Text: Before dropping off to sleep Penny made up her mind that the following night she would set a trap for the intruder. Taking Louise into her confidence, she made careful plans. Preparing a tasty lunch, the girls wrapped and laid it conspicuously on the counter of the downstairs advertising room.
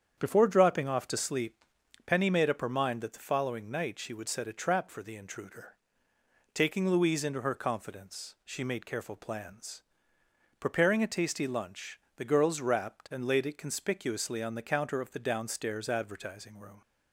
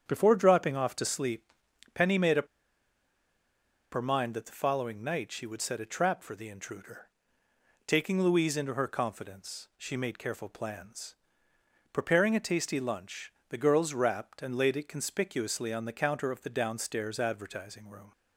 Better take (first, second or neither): first